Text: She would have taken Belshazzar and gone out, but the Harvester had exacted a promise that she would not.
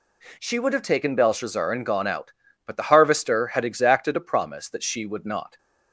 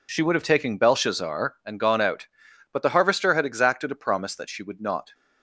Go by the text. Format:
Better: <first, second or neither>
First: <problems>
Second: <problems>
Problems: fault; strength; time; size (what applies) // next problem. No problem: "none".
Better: neither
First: none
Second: none